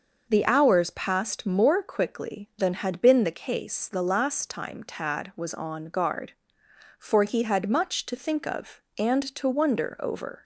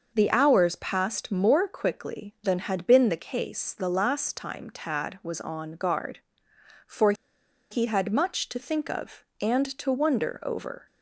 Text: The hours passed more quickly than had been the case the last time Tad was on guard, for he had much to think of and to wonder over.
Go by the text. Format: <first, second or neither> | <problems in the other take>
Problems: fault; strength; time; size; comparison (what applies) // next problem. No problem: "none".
first | pauses between "for" and "he"; noticeable; at 7.1 s; 0.57 s long